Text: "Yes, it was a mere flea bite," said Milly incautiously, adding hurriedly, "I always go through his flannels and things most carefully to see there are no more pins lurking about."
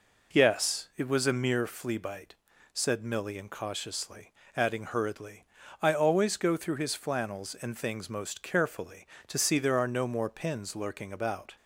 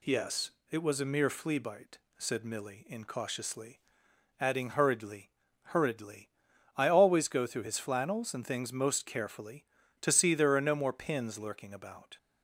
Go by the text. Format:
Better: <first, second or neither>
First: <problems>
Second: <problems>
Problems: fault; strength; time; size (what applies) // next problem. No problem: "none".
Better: first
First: none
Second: says "hurriedly" twice; at 5.6 s